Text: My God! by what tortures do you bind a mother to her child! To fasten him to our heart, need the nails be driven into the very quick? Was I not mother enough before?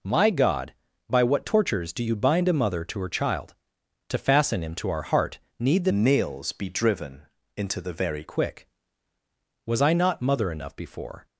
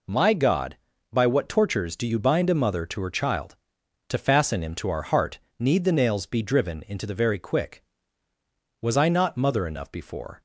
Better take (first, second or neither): second